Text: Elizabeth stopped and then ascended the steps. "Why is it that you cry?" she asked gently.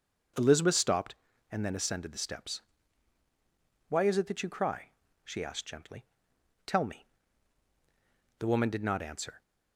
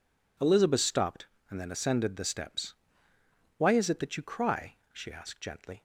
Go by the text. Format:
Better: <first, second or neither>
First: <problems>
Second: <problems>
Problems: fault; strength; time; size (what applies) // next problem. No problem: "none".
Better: second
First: goes on to say "Tell me The woman did not answer"; strong; from 6.6 s on; 2.7 s long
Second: none